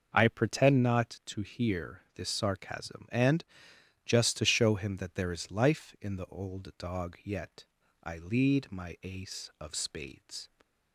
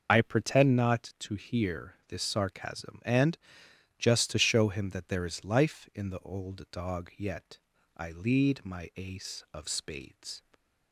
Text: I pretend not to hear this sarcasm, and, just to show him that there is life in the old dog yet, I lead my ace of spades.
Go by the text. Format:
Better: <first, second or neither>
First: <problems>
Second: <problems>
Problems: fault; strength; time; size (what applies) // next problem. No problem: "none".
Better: first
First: starts louder than the rest; until 1.1 s; 6 dB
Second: loses the start of "I"; at 0.0 s; 35 ms // starts louder than the rest; noticeable; until 1.1 s; 6 dB